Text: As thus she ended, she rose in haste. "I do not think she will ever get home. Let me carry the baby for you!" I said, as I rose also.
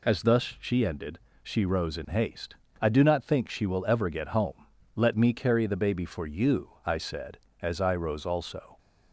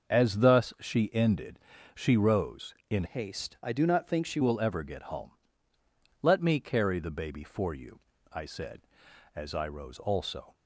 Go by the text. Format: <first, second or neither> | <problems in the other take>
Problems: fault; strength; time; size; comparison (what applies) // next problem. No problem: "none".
first | starts louder than the rest; until 1.1 s; 6.5 dB // changes voice from "haste" to "she"; from 3.0 to 4.3 s; 1.3 s long